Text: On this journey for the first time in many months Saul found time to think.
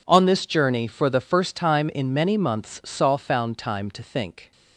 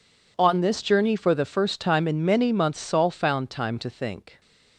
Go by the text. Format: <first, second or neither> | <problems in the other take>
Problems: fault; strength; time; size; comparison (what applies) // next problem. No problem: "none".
neither | none